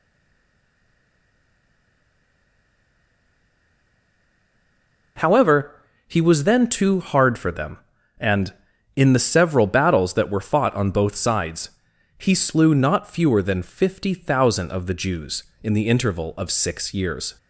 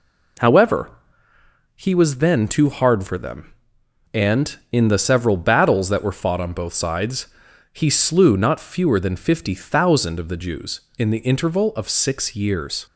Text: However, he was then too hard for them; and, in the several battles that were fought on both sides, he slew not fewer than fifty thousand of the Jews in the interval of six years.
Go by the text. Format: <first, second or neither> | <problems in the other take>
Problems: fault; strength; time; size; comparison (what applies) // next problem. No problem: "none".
second | stays silent before the first word; strong; until 5.1 s; 5.1 s long